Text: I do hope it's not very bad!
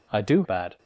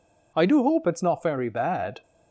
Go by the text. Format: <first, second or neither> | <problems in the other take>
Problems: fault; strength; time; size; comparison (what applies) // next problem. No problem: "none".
second | skips "hope it's not very"; at 0.4 s